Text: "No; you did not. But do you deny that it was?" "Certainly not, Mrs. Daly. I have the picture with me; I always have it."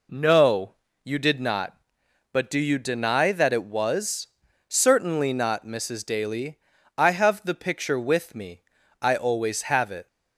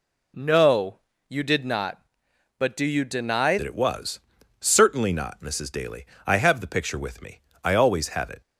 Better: first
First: none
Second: changes voice at "that"; from 3.5 s on; 4.9 s long

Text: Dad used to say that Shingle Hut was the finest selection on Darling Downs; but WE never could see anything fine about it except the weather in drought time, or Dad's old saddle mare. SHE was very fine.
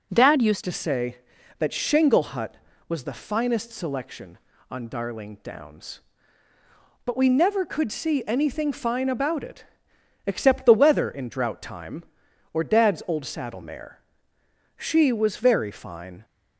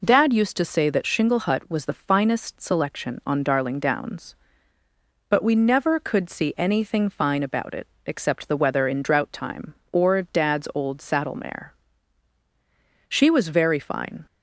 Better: second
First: changes voice at "to"; from 0.6 s on; 15.6 s long // pauses between "it" and "except"; noticeable; at 9.6 s; 0.60 s long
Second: pauses between "it" and "except"; slight; at 7.8 s; 0.18 s long

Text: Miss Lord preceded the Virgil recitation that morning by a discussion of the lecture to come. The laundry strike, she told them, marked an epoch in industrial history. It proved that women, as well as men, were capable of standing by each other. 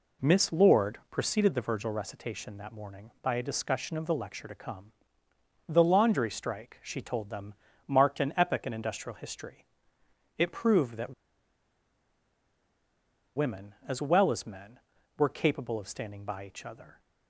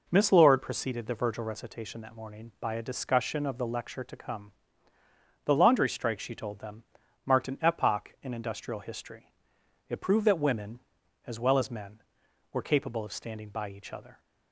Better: second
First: pauses between "that" and "women"; strong; at 11.1 s; 2.2 s long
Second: none

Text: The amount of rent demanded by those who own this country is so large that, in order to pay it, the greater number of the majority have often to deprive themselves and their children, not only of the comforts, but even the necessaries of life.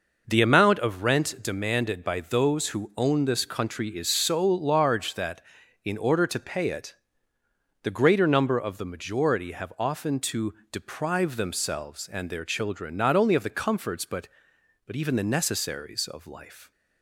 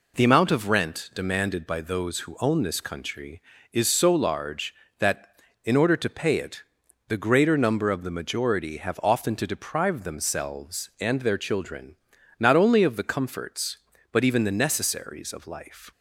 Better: second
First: pauses between "to" and "deprive"; slight; at 10.5 s; 0.16 s long // says "but" twice; at 14.8 s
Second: none

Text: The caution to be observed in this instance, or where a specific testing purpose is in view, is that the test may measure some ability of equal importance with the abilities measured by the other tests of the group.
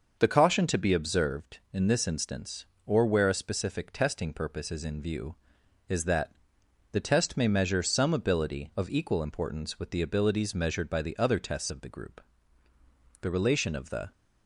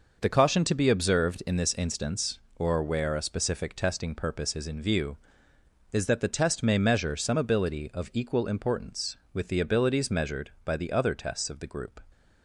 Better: second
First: starts louder than the rest; until 1.2 s; 6 dB // pauses between "that" and "the"; noticeable; at 6.3 s; 0.58 s long // goes on to say "The relation of the"; noticeable; from 13.2 s on; 0.90 s long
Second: none

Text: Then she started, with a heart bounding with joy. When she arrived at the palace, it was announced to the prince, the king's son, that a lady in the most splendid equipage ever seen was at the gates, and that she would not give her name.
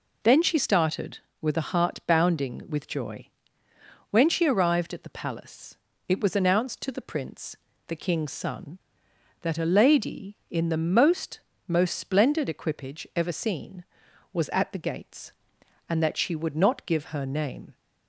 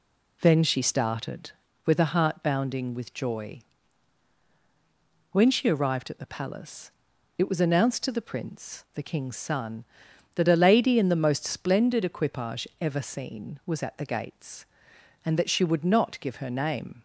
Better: second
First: says "most" twice; at 11.6 s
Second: none

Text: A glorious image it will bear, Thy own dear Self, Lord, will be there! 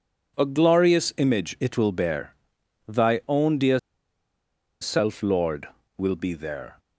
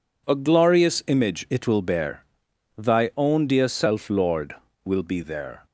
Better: second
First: pauses between "dear" and "Self"; at 3.7 s; 1.0 s long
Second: none

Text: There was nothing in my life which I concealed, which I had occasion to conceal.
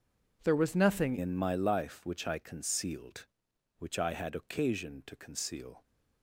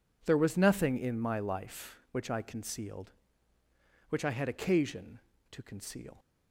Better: second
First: changes voice at "in"; from 1.1 s on; 4.7 s long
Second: none

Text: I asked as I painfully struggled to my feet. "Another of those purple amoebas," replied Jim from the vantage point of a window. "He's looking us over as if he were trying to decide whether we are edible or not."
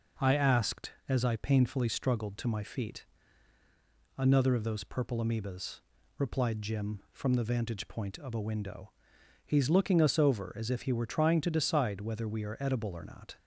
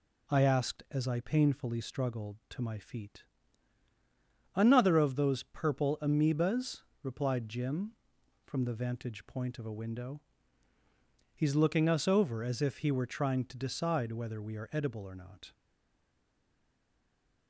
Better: first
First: none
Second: stays silent after the last word; noticeable; from 15.5 s on; 1.9 s long

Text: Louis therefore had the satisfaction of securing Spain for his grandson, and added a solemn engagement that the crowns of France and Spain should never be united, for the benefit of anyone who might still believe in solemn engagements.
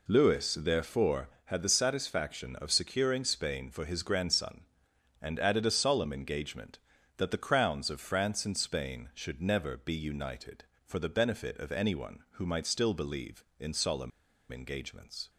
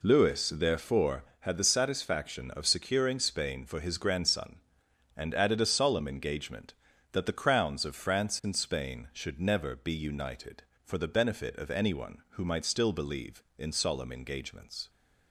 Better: second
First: pauses between "solemn" and "engagements"; at 14.1 s; 0.41 s long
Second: none

